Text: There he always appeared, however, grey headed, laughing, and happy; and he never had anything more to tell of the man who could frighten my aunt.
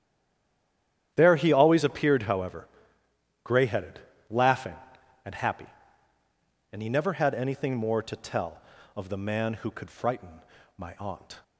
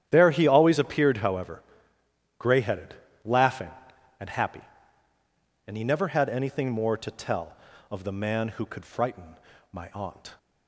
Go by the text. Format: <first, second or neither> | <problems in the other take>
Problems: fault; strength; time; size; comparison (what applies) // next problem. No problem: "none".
second | stays silent before the first word; until 1.1 s; 1.1 s long // starts louder than the rest; strong; until 2.1 s; 10.5 dB; strong in the second // pauses between "frighten" and "my"; slight; at 10.4 s; 0.34 s long; slight in the second